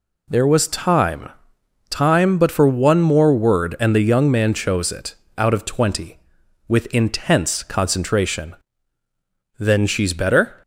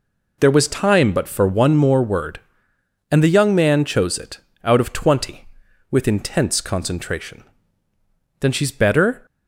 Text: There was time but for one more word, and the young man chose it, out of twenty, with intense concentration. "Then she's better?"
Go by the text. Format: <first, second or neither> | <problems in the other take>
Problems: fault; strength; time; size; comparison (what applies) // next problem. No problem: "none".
second | says "time" twice; at 1.8 s